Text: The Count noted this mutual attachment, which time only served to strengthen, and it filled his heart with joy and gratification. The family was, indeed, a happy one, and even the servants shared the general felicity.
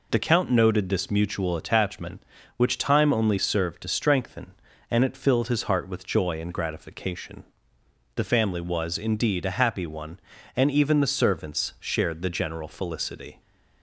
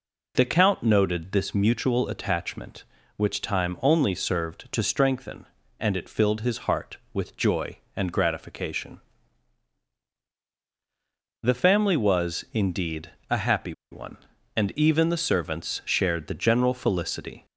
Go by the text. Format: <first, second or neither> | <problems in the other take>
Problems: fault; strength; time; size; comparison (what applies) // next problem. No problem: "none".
first | pauses between "happy" and "one"; slight; at 13.7 s; 0.19 s long